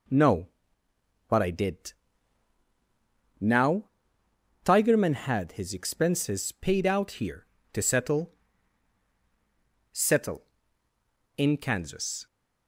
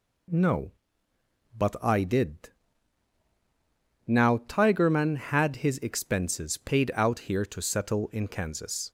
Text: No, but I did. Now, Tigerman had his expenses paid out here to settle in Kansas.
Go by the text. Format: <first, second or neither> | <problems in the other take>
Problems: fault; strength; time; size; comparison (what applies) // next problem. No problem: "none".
second | says "settle" twice; at 9.9 s